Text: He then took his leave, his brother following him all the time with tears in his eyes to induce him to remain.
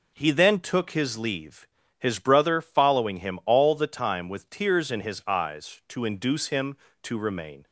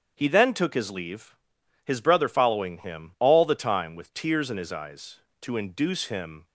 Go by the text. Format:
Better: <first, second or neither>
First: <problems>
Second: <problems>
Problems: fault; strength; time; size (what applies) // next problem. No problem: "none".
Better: first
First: none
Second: starts louder than the rest; strong; until 1.1 s; 8 dB // stops before "to remain"; at 6.4 s